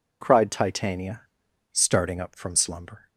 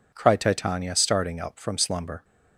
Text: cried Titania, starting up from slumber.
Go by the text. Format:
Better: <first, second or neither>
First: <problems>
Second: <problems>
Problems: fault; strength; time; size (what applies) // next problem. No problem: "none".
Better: neither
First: none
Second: none